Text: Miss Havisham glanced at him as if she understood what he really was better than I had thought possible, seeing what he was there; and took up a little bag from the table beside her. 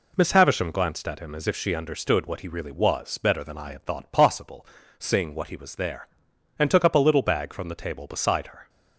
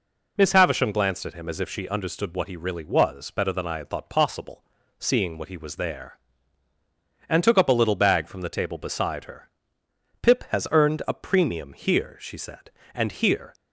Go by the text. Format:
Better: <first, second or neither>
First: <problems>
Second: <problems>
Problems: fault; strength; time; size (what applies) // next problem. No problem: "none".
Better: first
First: none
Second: goes on to say "Pip has earned a premium here she said and here"; strong; from 10.2 s on; 3.3 s long